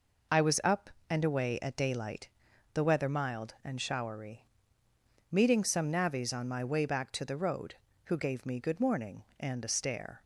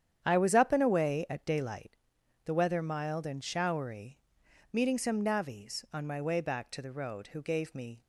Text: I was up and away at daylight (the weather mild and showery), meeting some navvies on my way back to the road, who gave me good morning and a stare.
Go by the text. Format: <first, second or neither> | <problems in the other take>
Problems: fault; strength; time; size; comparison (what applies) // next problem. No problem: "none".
first | starts louder than the rest; strong; until 1.2 s; 9.5 dB // stops before "good morning and a stare"; at 8.0 s